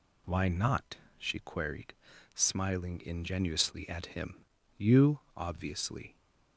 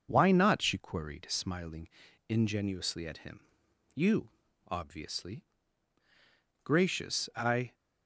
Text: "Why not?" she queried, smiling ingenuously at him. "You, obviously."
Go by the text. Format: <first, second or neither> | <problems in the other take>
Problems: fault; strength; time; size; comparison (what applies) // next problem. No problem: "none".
first | pauses between "smiling" and "ingenuously"; at 1.8 s; 0.40 s long // goes on to say "Gracious I"; noticeable; from 6.6 s on; 1.1 s long